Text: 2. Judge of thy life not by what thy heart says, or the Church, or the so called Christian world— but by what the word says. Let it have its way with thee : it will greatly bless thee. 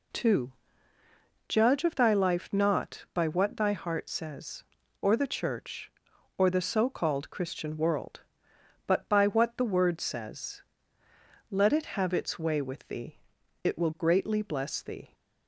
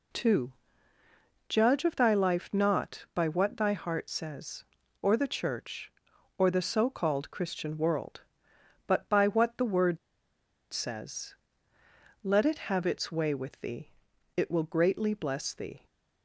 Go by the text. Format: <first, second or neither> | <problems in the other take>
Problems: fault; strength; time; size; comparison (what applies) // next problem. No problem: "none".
first | pauses between "word" and "says"; noticeable; at 9.9 s; 0.74 s long